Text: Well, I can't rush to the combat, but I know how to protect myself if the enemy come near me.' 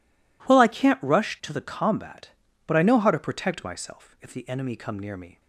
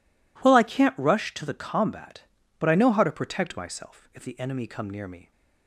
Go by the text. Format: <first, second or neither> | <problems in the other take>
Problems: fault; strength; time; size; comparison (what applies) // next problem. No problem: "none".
neither | none